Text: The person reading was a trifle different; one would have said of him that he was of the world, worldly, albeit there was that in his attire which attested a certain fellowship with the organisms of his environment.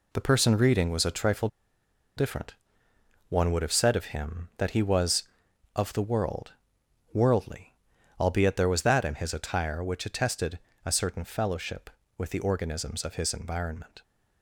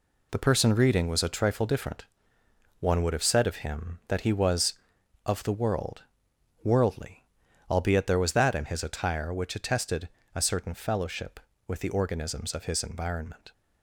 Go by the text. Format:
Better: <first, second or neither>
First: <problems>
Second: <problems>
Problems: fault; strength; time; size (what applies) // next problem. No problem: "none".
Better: second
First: pauses between "trifle" and "different"; noticeable; at 1.4 s; 0.69 s long // pauses between "attested" and "a"; slight; at 10.5 s; 0.26 s long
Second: pauses between "attested" and "a"; slight; at 10.0 s; 0.26 s long